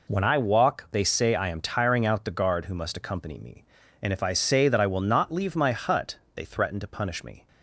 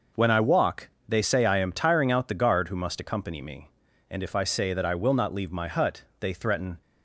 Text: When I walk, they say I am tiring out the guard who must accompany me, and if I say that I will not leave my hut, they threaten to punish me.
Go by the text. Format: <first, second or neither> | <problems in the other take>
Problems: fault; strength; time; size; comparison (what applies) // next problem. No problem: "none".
first | stops before "to punish me"; at 6.8 s